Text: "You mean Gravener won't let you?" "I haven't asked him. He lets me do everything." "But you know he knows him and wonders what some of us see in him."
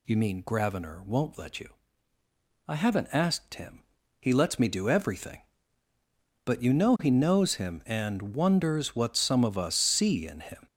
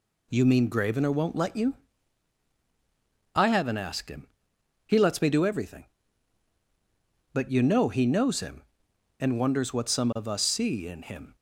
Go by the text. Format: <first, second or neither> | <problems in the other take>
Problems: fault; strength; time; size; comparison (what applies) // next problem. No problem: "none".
second | gets louder; throughout; 6.5 dB